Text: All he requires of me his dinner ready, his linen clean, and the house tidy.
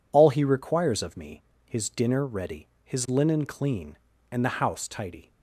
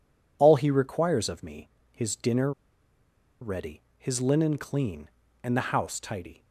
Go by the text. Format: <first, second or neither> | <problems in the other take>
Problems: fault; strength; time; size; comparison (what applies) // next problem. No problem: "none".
first | pauses between "me" and "his"; slight; at 1.6 s; 0.22 s long; slight in the first // pauses between "dinner" and "ready"; noticeable; at 2.5 s; 0.90 s long